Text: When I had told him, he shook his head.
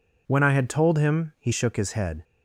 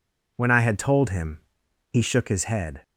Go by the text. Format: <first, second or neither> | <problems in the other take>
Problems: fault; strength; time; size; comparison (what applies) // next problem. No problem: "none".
neither | none